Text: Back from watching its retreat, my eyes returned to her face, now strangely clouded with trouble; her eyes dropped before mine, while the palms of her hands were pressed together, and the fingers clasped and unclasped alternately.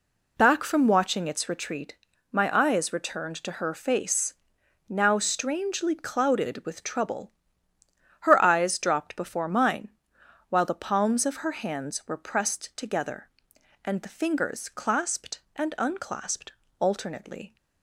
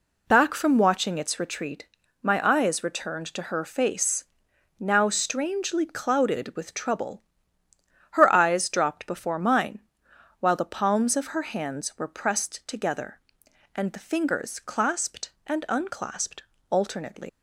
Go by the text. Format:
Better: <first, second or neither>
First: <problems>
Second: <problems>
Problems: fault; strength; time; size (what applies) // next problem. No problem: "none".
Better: first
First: pauses between "unclasped" and "alternately"; slight; at 16.5 s; 0.28 s long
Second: pauses between "unclasped" and "alternately"; slight; at 16.4 s; 0.28 s long // leaves "alternately" unfinished; at 17.2 s; 170 ms